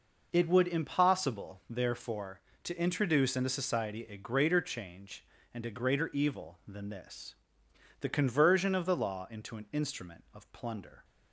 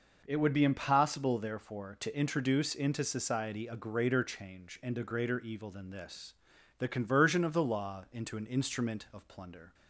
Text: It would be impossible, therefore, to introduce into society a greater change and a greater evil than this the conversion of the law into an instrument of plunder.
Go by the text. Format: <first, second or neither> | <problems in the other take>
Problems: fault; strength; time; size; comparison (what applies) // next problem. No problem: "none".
second | skips "be"; at 0.6 s // pauses between "this" and "the"; noticeable; at 7.3 s; 0.66 s long; also in the second